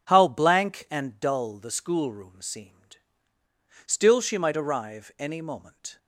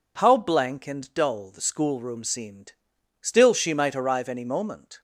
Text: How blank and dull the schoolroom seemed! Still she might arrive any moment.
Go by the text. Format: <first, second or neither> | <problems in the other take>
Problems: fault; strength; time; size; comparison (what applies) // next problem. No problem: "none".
neither | none